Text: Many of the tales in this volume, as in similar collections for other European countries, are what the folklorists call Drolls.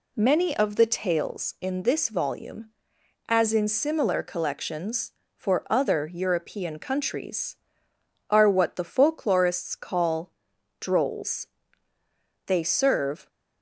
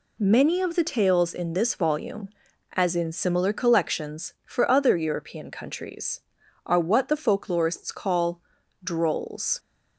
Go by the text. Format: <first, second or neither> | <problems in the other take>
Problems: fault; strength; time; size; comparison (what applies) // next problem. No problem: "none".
second | pauses between "call" and "Drolls"; noticeable; at 10.3 s; 0.48 s long; also in the second // goes on to say "They serve"; noticeable; from 12.4 s on; 0.82 s long